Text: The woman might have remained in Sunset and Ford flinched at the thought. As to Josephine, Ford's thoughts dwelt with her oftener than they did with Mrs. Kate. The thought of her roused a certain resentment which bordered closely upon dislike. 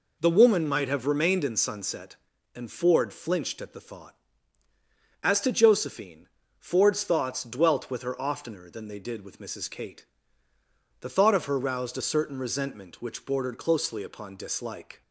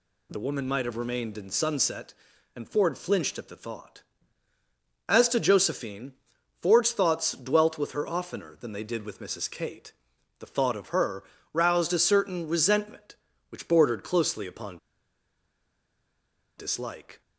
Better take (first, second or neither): first